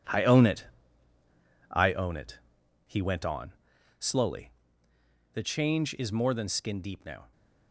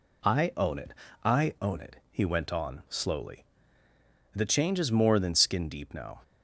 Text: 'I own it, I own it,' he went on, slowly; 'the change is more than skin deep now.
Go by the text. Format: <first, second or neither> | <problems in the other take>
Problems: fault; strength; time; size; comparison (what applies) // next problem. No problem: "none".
second | gets quieter; strong; throughout; 10.5 dB